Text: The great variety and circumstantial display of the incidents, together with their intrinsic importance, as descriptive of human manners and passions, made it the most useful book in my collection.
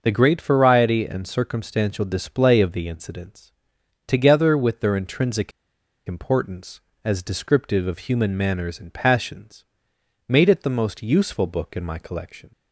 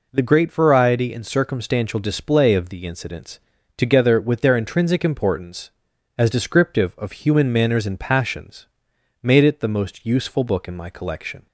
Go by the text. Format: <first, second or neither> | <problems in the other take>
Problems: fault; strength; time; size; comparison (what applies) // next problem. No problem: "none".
second | starts louder than the rest; noticeable; until 1.0 s; 6 dB // pauses between "intrinsic" and "importance"; noticeable; at 5.5 s; 0.56 s long